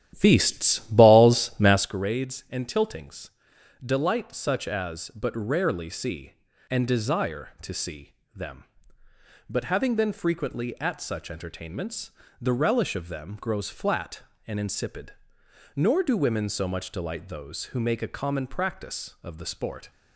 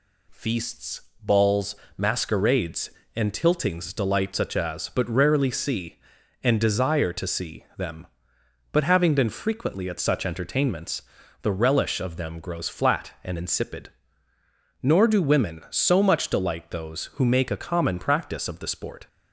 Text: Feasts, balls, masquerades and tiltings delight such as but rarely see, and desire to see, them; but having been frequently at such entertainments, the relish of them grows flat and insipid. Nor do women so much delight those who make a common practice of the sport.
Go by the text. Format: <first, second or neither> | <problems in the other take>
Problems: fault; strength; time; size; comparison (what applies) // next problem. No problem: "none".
second | starts louder than the rest; strong; until 2.0 s; 12 dB // pauses between "tiltings" and "delight"; noticeable; at 3.3 s; 0.54 s long